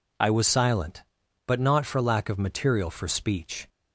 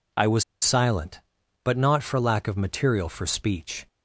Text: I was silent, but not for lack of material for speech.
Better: first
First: none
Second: pauses between "was" and "silent"; slight; at 0.4 s; 0.19 s long

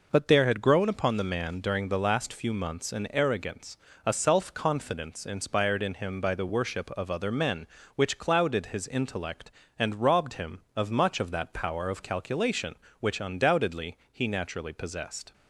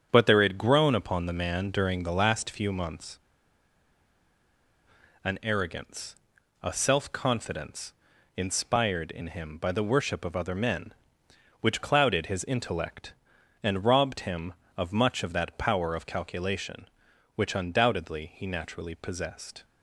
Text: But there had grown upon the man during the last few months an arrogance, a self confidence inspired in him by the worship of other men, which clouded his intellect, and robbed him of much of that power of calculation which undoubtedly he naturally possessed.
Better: first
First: none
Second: starts louder than the rest; strong; until 1.1 s; 7.5 dB // pauses between "months" and "an"; strong; at 3.1 s; 2.0 s long // pauses between "confidence" and "inspired"; at 7.9 s; 0.44 s long

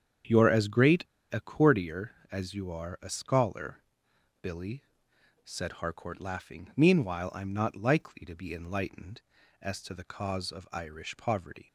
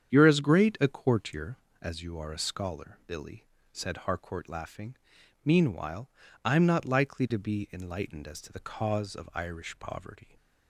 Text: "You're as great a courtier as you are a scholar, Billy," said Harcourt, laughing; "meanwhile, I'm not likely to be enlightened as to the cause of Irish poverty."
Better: second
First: starts louder than the rest; strong; until 1.5 s; 8 dB // pauses between "great" and "a"; slight; at 1.0 s; 0.27 s long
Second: starts louder than the rest; strong; until 1.1 s; 8.5 dB

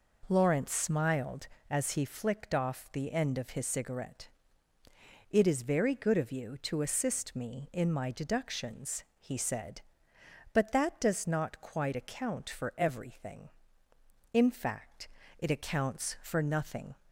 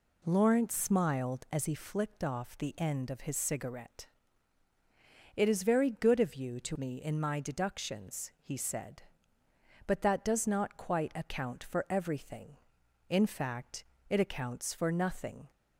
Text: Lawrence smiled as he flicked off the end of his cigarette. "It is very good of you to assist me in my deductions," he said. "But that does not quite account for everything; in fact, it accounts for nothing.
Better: first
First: none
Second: skips "assist"; at 6.7 s

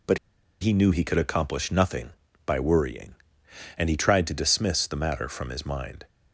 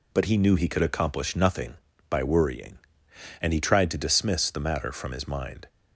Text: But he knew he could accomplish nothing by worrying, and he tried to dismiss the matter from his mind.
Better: second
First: pauses between "But" and "he"; at 0.1 s; 0.43 s long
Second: none

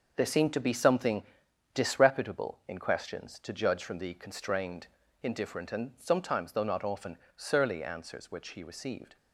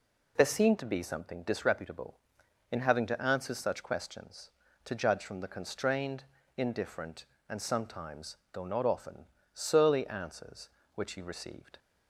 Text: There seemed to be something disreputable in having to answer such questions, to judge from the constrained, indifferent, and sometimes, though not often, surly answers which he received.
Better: second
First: starts louder than the rest; noticeable; until 1.1 s; 6 dB // pauses between "something" and "disreputable"; noticeable; at 1.2 s; 0.50 s long // skips "having to answer such"; at 2.7 s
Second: none

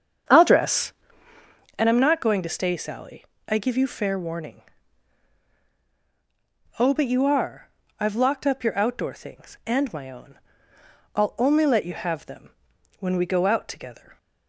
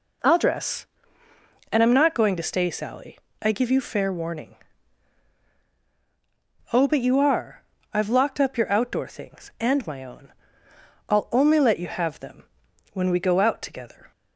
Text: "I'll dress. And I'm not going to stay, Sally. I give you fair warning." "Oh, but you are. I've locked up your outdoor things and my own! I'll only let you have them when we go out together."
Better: second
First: starts louder than the rest; strong; until 1.7 s; 8 dB // pauses between "them" and "when"; noticeable; at 12.4 s; 0.50 s long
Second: pauses between "them" and "when"; noticeable; at 12.4 s; 0.50 s long

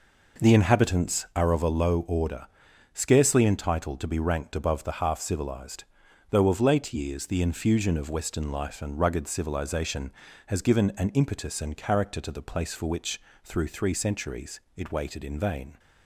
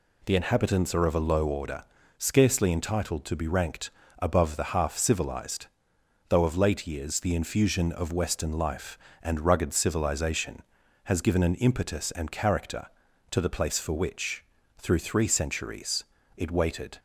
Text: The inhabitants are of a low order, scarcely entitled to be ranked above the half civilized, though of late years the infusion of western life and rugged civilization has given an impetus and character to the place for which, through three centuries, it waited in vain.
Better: first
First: none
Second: pauses between "ranked" and "above"; slight; at 3.9 s; 0.28 s long // stops before "in vain"; at 16.9 s

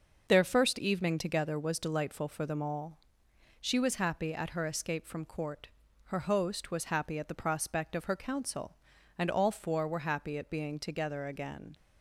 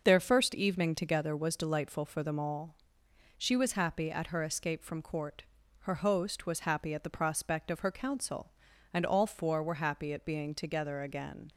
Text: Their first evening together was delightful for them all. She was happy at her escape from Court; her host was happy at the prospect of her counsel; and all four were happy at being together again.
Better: neither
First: starts louder than the rest; noticeable; until 1.3 s; 6 dB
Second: starts louder than the rest; noticeable; until 1.0 s; 6 dB

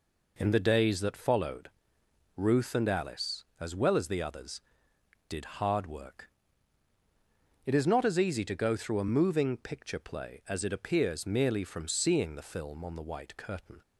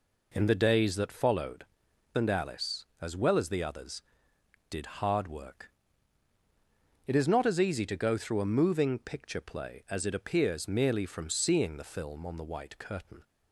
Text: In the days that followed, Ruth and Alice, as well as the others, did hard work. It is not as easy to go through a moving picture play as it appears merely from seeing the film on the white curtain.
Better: first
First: none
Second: skips "Ruth"; at 1.9 s

